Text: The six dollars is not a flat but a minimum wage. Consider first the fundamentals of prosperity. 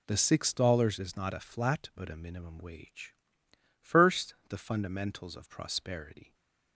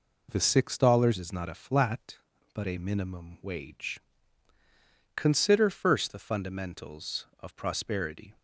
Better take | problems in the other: second | skips "Consider"; at 3.4 s // stays silent after the last word; slight; from 6.2 s on; 0.5 s long

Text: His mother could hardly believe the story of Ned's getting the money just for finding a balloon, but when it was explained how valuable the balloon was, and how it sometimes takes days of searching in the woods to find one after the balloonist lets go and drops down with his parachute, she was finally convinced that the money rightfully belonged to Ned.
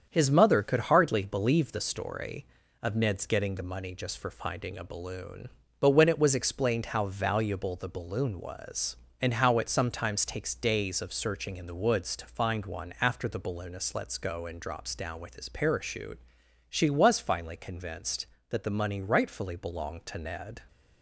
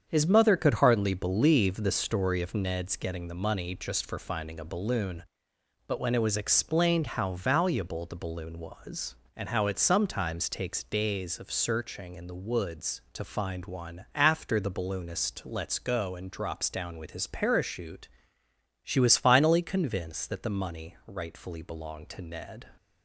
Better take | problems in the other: neither | starts louder than the rest; strong; the same in both

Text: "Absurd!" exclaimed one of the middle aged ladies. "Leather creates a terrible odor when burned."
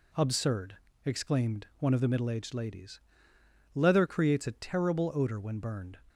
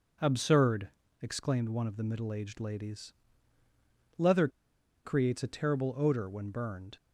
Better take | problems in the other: first | pauses between "Leather" and "creates"; noticeable; at 4.4 s; 0.56 s long

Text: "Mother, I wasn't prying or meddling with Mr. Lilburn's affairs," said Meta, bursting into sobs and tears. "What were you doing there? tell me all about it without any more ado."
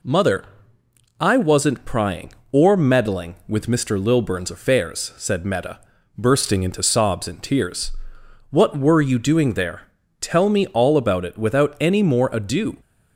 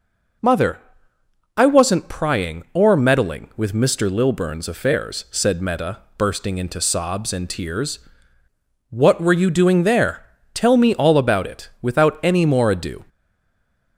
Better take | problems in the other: first | stays silent after the last word; slight; from 13.0 s on; 0.9 s long

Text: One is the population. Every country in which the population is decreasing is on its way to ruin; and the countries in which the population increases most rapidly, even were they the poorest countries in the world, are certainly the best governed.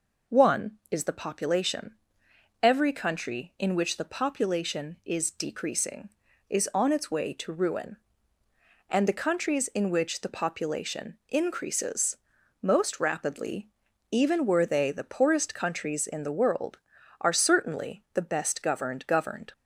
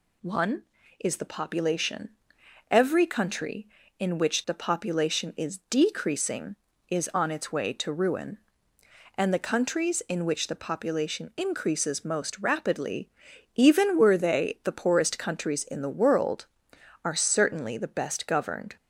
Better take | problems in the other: second | pauses between "increases" and "most"; noticeable; at 12.1 s; 0.46 s long // says "governed" twice; at 19.0 s

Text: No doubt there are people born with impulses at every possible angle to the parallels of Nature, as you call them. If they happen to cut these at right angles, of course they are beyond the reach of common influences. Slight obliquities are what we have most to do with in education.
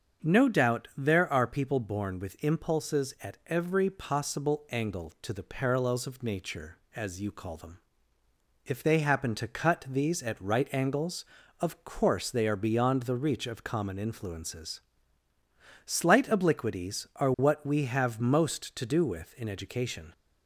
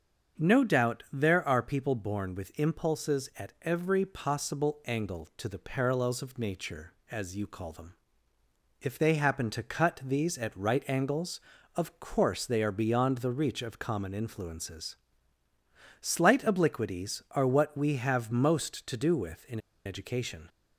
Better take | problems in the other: first | starts louder than the rest; until 1.4 s; 6.5 dB; also in the first // pauses between "in" and "education"; slight; at 19.5 s; 0.26 s long

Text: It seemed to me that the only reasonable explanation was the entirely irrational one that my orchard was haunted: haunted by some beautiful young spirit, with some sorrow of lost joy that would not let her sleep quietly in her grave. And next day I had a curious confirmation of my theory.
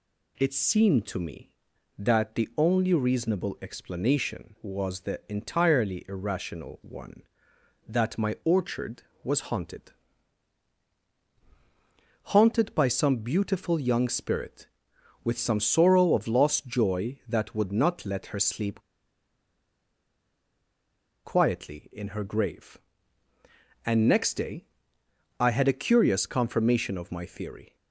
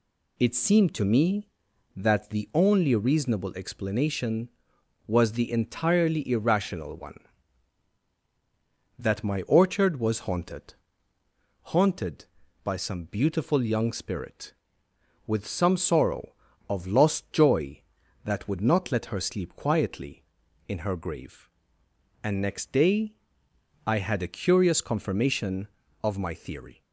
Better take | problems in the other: second | pauses between "sleep" and "quietly"; strong; at 18.8 s; 2.4 s long // pauses between "day" and "I"; noticeable; at 24.6 s; 0.74 s long; noticeable in the second

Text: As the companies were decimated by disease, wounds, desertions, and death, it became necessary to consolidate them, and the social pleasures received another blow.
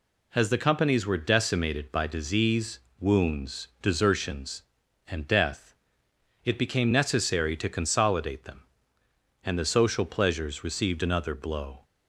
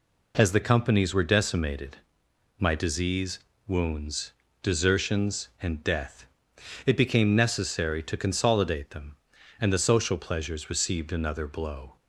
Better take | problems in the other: first | says "my" for "by"; at 2.5 s

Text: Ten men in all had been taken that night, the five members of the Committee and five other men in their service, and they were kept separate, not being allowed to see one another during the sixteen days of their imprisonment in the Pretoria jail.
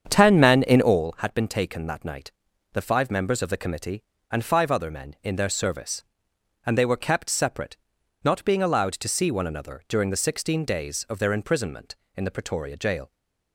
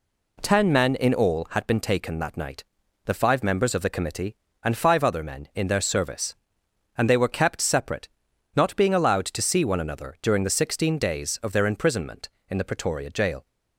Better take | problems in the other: second | starts louder than the rest; strong; until 1.1 s; 7.5 dB

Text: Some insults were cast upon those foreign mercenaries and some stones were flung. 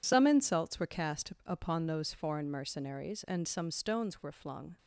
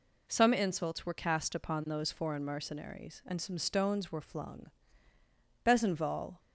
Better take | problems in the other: first | goes on to say "Besenval"; noticeable; from 5.6 s on; 0.74 s long

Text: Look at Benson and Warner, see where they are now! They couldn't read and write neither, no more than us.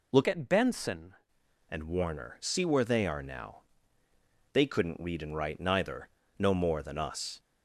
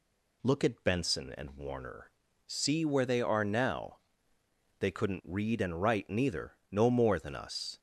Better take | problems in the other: second | changes voice from "at" to "Benson"; from 0.2 to 1.1 s; 0.9 s long

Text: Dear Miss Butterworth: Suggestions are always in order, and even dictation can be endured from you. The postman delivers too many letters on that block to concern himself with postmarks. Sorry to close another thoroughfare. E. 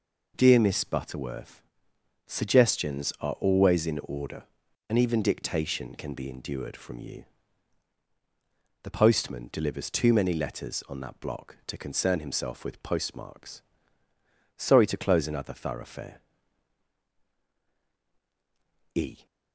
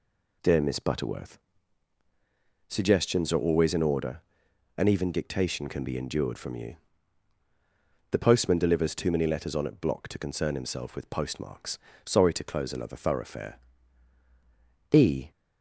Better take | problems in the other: first | says "at" for "that"; at 9.6 s

